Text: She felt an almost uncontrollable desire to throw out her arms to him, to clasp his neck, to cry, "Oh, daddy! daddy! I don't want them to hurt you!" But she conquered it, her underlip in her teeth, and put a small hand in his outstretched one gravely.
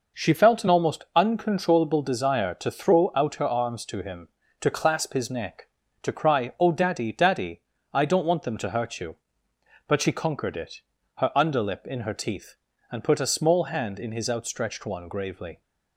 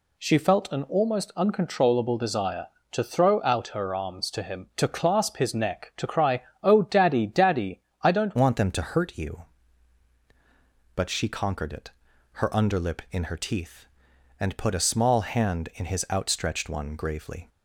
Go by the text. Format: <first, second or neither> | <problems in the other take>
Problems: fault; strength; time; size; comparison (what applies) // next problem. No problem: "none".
first | changes voice at "want"; from 8.3 s on; 9.1 s long